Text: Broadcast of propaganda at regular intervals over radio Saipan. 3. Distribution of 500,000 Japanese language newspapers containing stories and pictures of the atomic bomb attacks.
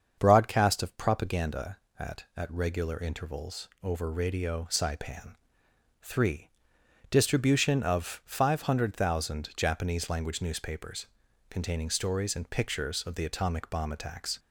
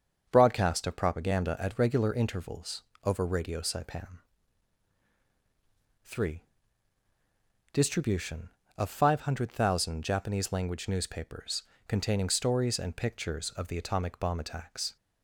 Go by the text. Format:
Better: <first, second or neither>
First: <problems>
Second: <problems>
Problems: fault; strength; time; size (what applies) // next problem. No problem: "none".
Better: second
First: starts louder than the rest; until 1.2 s; 7 dB // says "at" twice; at 2.3 s // pauses between "intervals" and "over"; slight; at 3.6 s; 0.16 s long // pauses between "newspapers" and "containing"; noticeable; at 11.0 s; 0.46 s long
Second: starts louder than the rest; until 1.3 s; 7 dB // pauses between "intervals" and "over"; slight; at 2.8 s; 0.22 s long // pauses between "newspapers" and "containing"; slight; at 11.6 s; 0.24 s long